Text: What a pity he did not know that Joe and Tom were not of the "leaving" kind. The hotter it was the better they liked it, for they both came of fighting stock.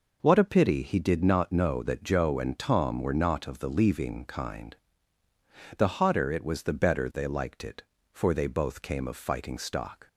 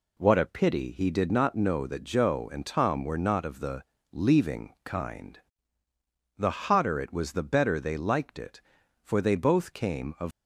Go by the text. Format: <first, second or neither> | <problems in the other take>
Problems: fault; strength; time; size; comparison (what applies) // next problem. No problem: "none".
first | pauses between "the" and "leaving"; slight; at 3.8 s; 0.30 s long // stops before "fighting stock"; at 10.3 s